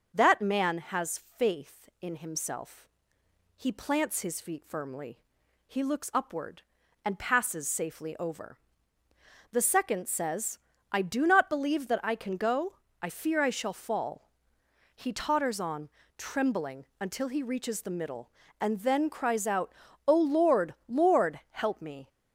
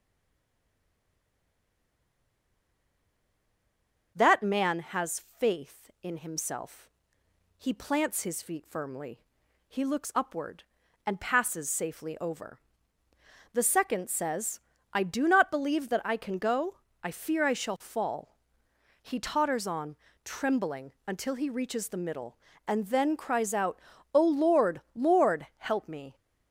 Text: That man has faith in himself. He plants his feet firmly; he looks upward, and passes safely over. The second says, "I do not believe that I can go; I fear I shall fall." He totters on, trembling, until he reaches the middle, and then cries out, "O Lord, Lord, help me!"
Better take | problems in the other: first | stays silent before the first word; strong; until 4.1 s; 4.1 s long // pauses between "has" and "faith"; slight; at 5.2 s; 0.18 s long; slight in the first

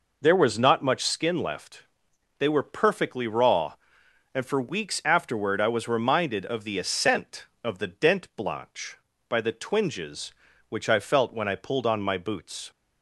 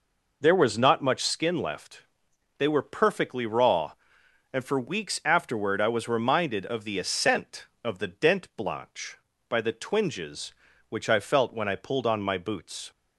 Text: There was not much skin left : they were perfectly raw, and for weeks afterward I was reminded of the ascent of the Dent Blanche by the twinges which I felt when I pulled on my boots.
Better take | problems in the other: neither | none

